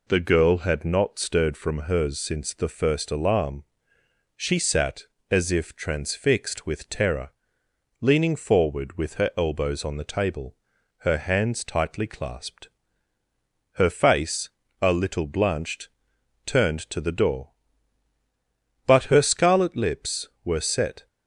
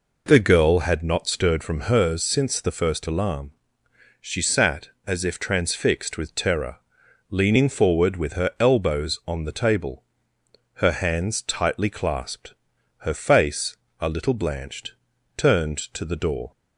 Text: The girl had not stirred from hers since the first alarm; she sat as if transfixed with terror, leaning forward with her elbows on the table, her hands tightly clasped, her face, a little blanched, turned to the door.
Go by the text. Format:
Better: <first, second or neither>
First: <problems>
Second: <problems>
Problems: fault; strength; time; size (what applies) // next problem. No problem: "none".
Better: second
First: goes on to say "But her scarlet lips were set"; strong; from 18.8 s on; 2.2 s long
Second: none